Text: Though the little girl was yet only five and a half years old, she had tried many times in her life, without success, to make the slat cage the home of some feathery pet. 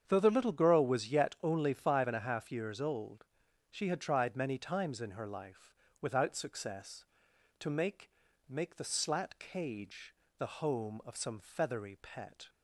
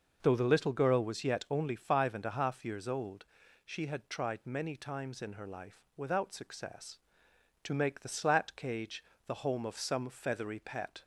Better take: second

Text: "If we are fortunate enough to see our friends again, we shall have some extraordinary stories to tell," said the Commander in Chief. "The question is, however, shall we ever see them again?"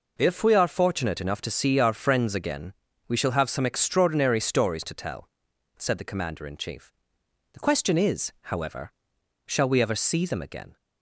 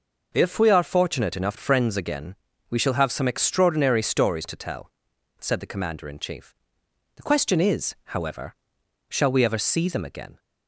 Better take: first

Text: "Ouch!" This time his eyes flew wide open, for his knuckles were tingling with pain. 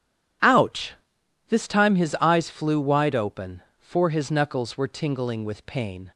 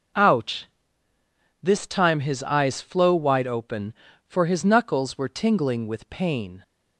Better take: first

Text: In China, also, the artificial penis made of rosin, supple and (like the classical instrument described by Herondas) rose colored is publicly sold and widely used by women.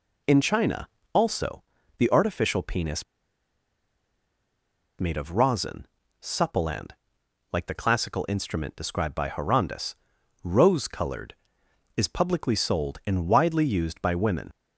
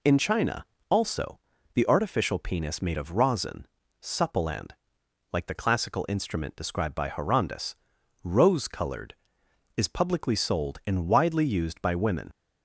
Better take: second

